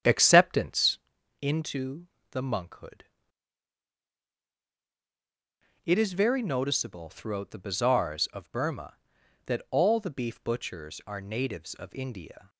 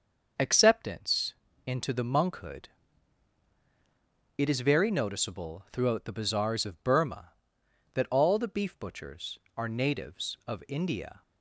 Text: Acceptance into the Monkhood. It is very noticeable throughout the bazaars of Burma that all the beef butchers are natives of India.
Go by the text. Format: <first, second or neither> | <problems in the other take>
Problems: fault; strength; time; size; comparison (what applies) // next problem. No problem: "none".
second | starts louder than the rest; strong; until 1.1 s; 9 dB // pauses between "Acceptance" and "into"; at 0.9 s; 0.44 s long; slight in the second // pauses between "into" and "the"; slight; at 2.0 s; 0.24 s long